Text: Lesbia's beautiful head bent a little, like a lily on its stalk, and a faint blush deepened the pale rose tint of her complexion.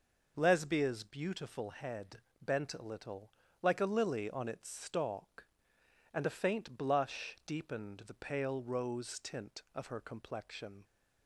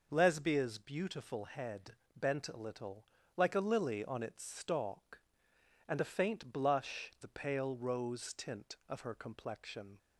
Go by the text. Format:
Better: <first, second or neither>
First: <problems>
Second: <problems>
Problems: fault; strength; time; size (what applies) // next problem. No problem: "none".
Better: first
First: pauses between "head" and "bent"; slight; at 2.2 s; 0.20 s long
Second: pauses between "head" and "bent"; slight; at 1.9 s; 0.20 s long // skips "deepened"; at 7.1 s